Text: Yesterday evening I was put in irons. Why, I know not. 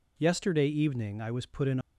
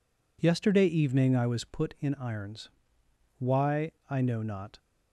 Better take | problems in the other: second | stops before "irons Why I know not"; at 1.8 s

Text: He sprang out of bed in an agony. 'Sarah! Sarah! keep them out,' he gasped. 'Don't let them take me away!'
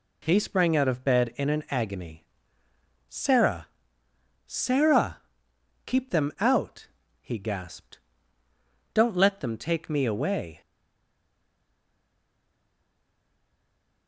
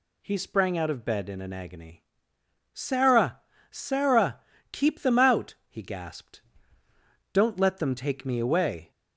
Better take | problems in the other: second | stays silent after the last word; strong; from 10.6 s on; 3.4 s long

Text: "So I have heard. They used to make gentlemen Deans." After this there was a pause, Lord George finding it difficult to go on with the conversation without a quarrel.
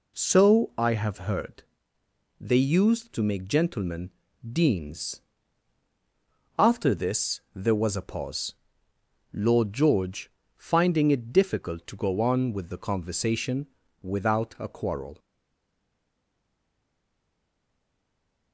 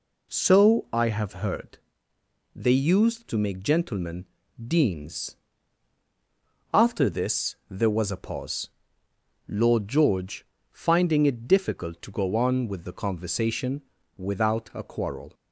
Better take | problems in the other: second | pauses between "gentlemen" and "Deans"; at 4.1 s; 0.38 s long; also in the second // pauses between "George" and "finding"; slight; at 10.3 s; 0.26 s long; slight in the second // pauses between "conversation" and "without"; slight; at 13.6 s; 0.36 s long; slight in the second // stays silent after the last word; strong; from 15.1 s on; 3.4 s long

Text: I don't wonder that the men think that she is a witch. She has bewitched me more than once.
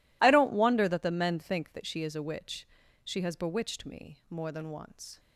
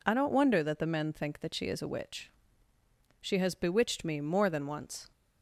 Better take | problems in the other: neither | none

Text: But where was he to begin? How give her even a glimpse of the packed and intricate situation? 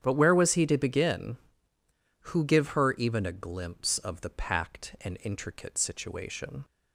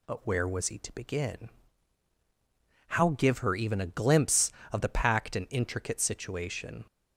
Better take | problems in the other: second | starts louder than the rest; strong; until 1.0 s; 9.5 dB // says "Who" for "How"; at 2.2 s

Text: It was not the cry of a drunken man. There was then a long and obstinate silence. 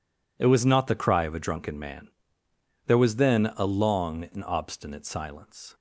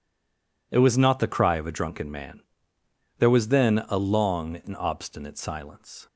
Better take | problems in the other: first | stays silent before the first word; slight; until 0.7 s; 0.7 s long

